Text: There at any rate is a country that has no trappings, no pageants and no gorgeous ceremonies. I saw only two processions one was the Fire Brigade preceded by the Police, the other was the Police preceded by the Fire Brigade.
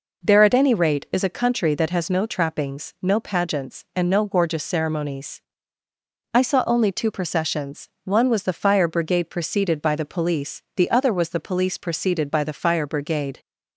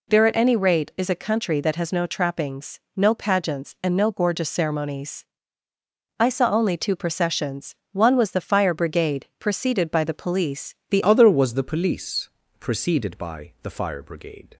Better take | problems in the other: first | pauses between "processions" and "one"; slight; at 7.7 s; 0.16 s long; slight in the first // changes voice at "other"; from 11.0 s on; 3.5 s long // pauses between "Police" and "preceded"; slight; at 12.2 s; 0.30 s long

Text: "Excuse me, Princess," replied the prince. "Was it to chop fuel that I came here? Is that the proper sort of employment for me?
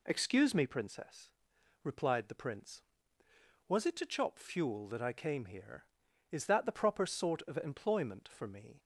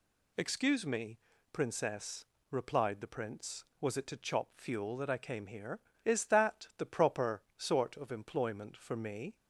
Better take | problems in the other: neither | none

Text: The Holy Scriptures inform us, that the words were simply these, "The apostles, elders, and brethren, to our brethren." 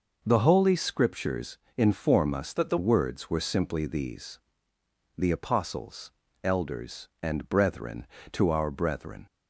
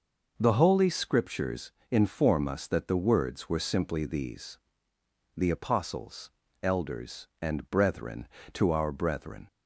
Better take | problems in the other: second | pauses between "Scriptures" and "inform"; slight; at 1.5 s; 0.18 s long; slight in the second // changes voice from "that" to "the"; from 2.5 to 2.7 s; 0.2 s long

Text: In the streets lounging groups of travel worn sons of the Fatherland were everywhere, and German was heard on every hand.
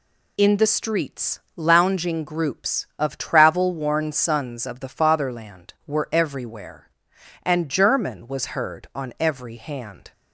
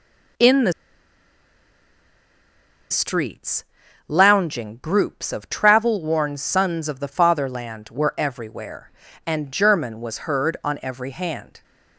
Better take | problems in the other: first | pauses between "the" and "streets"; strong; at 0.7 s; 2.1 s long // pauses between "streets" and "lounging"; at 3.6 s; 0.42 s long; slight in the first

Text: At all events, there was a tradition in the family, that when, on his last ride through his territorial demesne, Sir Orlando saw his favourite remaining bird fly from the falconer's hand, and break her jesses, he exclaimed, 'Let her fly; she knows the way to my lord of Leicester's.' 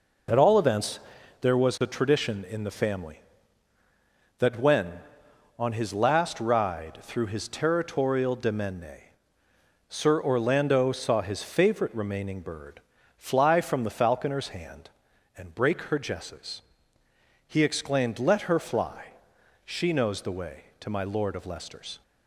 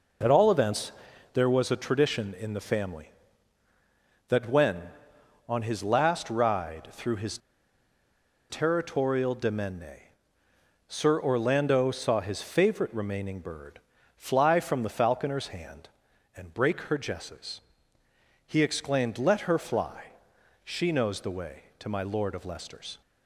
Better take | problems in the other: first | pauses between "his" and "territorial"; at 7.3 s; 1.1 s long // pauses between "bird" and "fly"; at 13.7 s; 0.38 s long; also in the first

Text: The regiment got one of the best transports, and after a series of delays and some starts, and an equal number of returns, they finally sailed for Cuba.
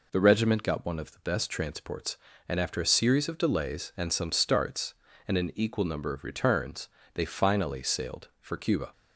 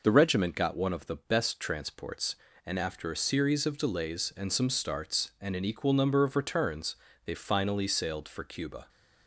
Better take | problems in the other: neither | none

